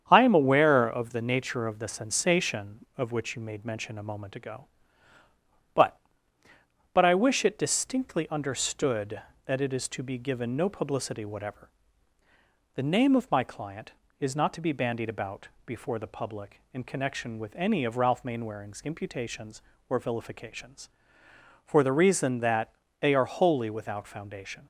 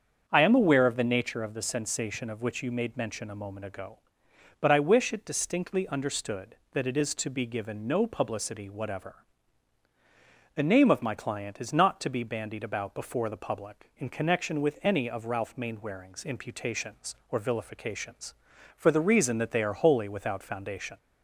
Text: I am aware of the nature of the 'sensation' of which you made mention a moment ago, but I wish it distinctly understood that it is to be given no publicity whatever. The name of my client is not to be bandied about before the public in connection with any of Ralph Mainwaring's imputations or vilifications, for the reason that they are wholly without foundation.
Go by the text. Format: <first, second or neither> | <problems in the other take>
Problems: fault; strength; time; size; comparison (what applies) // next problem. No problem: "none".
second | starts louder than the rest; strong; until 1.1 s; 8 dB; strong in the second // says "but" twice; at 6.9 s // pauses between "about" and "before"; slight; at 15.4 s; 0.18 s long // pauses between "that" and "they"; slight; at 22.7 s; 0.26 s long